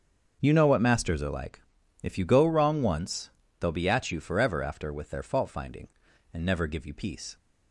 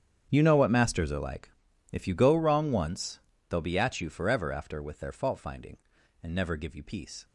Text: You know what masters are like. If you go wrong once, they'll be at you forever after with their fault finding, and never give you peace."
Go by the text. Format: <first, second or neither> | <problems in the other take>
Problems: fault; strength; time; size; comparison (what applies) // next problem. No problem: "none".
first | gets quieter; strong; throughout; 17.5 dB // starts louder than the rest; strong; until 1.3 s; 8.5 dB; also in the first